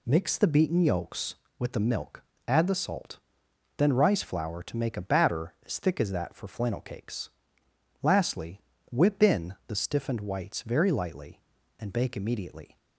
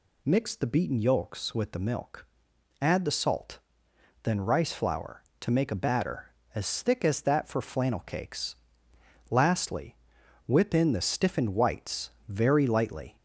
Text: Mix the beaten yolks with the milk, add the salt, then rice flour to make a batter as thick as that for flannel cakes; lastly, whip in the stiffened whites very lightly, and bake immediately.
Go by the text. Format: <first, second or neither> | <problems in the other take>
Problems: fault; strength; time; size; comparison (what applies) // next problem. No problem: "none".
first | pauses between "whites" and "very"; slight; at 12.0 s; 0.18 s long // stops before "and bake immediately"; at 13.1 s